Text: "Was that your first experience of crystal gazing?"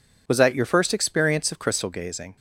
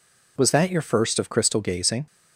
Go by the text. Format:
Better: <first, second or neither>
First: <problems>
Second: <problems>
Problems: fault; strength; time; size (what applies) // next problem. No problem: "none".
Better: first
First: none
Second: skips "experience"; at 1.1 s